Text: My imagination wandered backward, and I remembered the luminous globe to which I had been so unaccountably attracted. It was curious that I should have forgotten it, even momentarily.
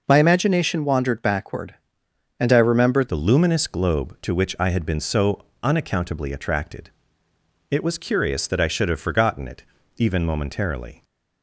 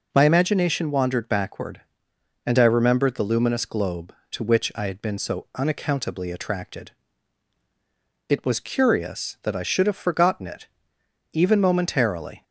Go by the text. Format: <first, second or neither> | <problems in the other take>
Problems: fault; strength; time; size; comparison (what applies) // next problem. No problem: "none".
second | changes voice at "the"; from 3.0 s on; 8.0 s long // pauses between "so" and "unaccountably"; slight; at 5.4 s; 0.18 s long